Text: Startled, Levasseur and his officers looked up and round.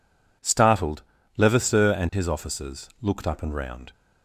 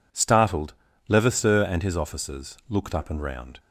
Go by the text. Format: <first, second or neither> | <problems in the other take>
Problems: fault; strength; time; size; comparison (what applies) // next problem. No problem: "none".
neither | none